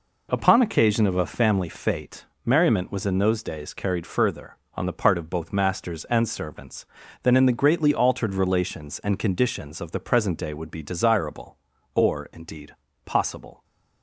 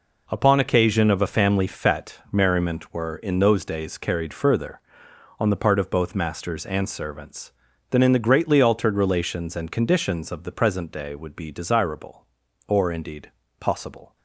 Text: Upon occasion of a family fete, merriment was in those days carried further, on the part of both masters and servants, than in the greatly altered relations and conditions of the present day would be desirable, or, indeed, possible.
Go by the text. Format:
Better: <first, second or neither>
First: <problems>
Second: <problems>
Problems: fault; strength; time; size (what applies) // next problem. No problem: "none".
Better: first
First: none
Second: says "were" for "was"; at 2.9 s